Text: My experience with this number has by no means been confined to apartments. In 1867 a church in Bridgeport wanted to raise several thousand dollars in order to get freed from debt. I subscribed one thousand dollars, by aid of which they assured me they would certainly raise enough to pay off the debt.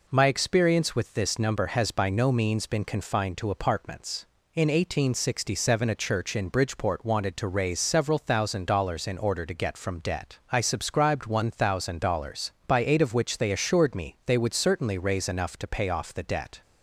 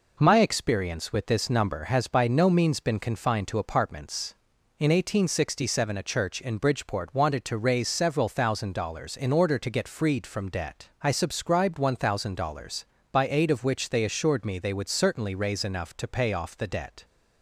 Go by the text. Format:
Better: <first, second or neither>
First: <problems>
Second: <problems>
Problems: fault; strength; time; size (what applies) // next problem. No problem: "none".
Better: second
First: skips "freed"; at 9.7 s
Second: none